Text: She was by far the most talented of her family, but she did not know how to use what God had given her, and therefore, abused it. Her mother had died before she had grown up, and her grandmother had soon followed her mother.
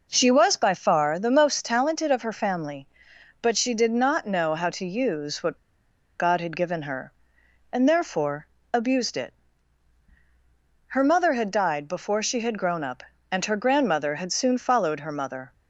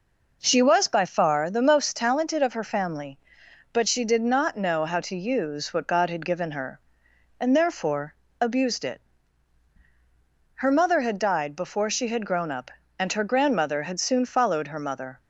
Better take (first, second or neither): second